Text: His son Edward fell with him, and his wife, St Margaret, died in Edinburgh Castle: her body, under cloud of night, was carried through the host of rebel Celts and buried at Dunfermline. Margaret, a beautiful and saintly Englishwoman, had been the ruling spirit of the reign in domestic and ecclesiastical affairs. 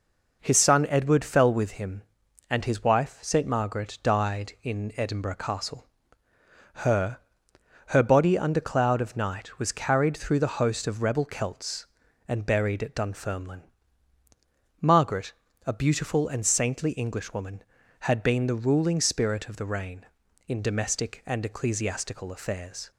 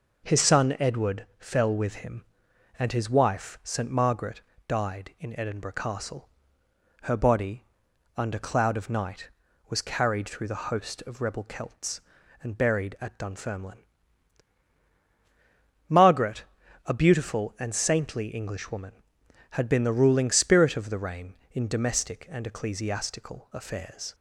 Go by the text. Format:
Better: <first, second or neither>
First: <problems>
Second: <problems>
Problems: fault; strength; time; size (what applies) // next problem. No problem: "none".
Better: second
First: says "her" twice; at 7.8 s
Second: none